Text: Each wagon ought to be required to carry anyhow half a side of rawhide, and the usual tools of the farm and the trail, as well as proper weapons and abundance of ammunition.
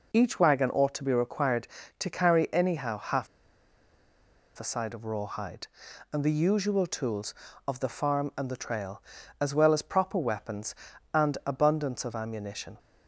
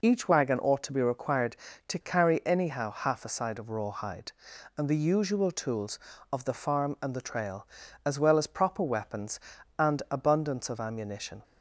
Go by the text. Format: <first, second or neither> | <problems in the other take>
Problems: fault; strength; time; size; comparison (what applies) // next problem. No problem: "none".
second | pauses between "half" and "a"; strong; at 3.2 s; 1.3 s long